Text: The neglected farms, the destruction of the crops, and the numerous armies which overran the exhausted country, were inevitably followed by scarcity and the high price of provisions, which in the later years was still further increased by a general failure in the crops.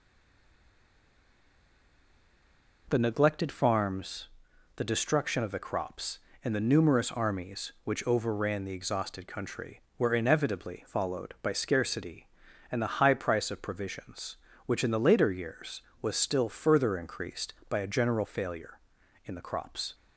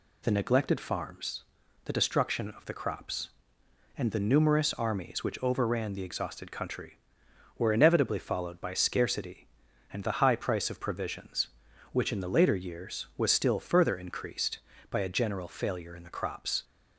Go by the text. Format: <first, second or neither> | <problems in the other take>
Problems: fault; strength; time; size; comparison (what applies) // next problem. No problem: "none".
second | stays silent before the first word; strong; until 2.8 s; 2.8 s long